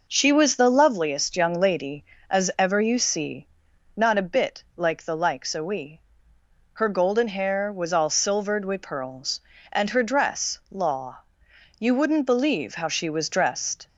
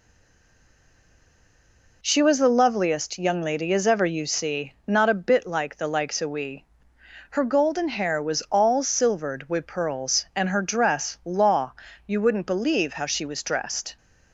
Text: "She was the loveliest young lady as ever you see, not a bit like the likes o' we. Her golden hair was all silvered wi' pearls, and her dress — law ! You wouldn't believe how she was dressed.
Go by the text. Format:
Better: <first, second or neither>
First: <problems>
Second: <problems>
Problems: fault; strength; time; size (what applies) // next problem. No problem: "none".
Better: first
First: none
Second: stays silent before the first word; noticeable; until 2.0 s; 2.0 s long